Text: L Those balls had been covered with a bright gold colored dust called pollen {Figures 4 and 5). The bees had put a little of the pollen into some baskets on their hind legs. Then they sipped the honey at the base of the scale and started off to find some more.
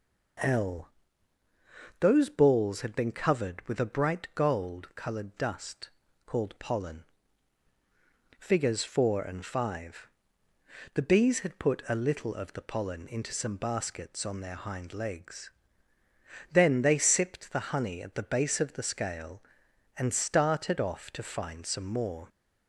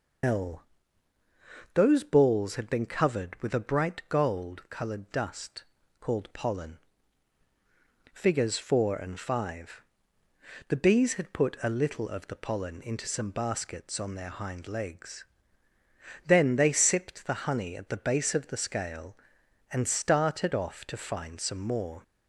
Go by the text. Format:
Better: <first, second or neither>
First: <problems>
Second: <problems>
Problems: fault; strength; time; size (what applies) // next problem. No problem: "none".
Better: first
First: pauses between "L" and "Those"; at 0.8 s; 1.1 s long // pauses between "dust" and "called"; slight; at 5.9 s; 0.36 s long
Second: loses the start of "L"; at 0.2 s; 120 ms // pauses between "L" and "Those"; at 0.6 s; 1.1 s long // pauses between "dust" and "called"; slight; at 5.6 s; 0.36 s long